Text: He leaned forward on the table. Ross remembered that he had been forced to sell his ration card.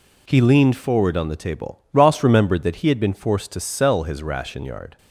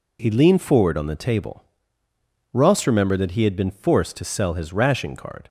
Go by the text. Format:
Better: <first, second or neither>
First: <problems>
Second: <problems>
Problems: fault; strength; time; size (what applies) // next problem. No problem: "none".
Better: second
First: says "yard" for "card"; at 4.6 s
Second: none